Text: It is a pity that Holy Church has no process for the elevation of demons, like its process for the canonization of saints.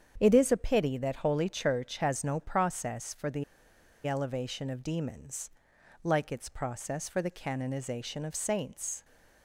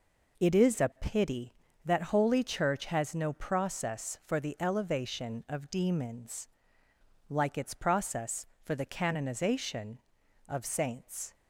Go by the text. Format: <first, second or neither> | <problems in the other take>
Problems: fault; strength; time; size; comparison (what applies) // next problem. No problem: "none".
second | starts louder than the rest; strong; until 1.1 s; 8 dB // pauses between "the" and "elevation"; noticeable; at 3.4 s; 0.62 s long